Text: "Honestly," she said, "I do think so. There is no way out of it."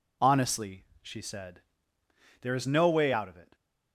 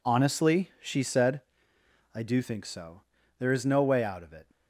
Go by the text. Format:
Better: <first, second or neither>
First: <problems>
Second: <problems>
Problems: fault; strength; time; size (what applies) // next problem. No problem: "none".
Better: second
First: skips "I do think so"; at 2.0 s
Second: none